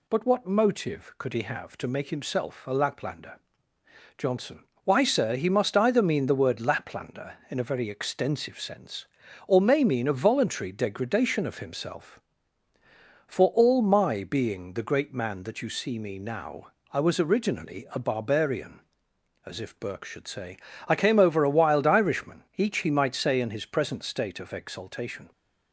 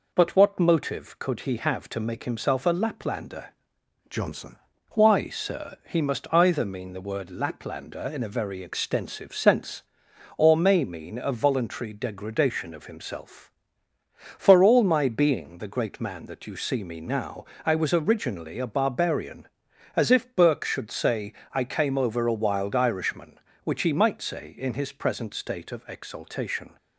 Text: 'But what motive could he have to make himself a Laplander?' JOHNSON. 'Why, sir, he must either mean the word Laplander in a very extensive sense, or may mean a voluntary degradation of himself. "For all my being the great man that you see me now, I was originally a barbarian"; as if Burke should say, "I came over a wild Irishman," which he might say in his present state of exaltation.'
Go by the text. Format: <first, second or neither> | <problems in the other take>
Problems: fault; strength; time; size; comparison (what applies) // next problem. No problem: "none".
second | says "each" for "which"; at 22.5 s